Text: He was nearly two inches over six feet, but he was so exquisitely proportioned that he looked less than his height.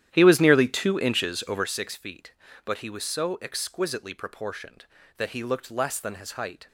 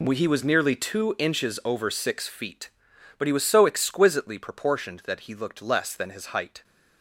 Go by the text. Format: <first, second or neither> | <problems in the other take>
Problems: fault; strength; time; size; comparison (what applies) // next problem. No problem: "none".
second | starts louder than the rest; strong; until 1.7 s; 11 dB